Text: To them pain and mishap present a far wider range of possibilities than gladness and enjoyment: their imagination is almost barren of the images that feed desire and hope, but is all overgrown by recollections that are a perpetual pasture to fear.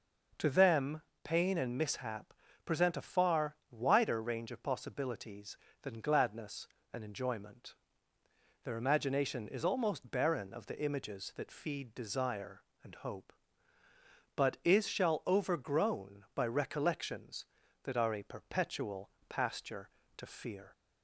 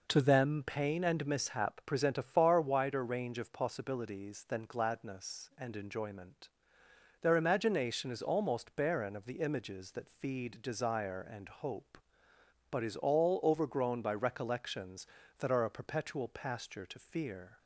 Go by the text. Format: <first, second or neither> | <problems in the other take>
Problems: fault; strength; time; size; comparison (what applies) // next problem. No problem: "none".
second | pauses between "them" and "pain"; slight; at 1.0 s; 0.22 s long // pauses between "mishap" and "present"; slight; at 2.3 s; 0.32 s long // pauses between "far" and "wider"; slight; at 3.5 s; 0.16 s long // says "shall" for "all"; at 14.8 s // pauses between "perpetual" and "pasture"; slight; at 19.1 s; 0.18 s long